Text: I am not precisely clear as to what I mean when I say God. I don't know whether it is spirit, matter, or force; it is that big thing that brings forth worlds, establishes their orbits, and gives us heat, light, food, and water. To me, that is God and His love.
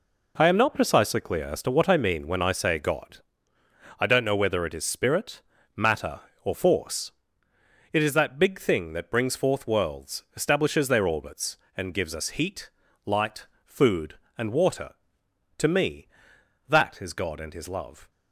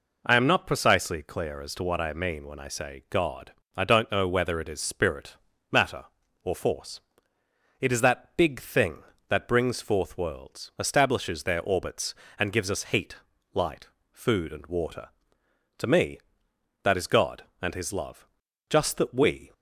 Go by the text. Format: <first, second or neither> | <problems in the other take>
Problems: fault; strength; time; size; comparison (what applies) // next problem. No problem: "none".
first | goes on to say "Just that we"; noticeable; from 18.6 s on; 0.84 s long